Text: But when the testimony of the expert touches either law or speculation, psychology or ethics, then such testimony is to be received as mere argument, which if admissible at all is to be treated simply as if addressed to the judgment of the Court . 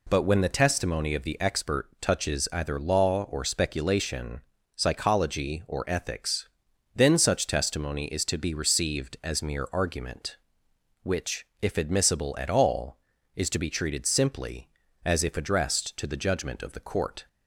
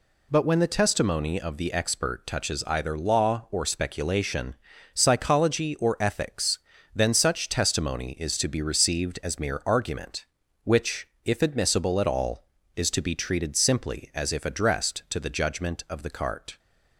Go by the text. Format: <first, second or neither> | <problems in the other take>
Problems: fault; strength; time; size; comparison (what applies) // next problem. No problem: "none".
first | pauses between "which" and "if"; slight; at 11.0 s; 0.18 s long; slight in the first // says "Cart" for "Court"; at 16.1 s